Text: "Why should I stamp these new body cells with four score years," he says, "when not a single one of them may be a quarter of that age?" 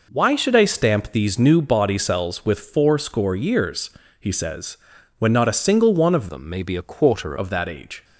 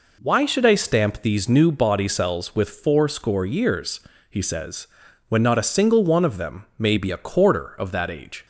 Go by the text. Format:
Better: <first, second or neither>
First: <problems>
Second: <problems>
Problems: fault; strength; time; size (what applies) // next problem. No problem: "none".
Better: second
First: changes voice from "them" to "quarter"; from 6.2 to 7.3 s; 1.1 s long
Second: none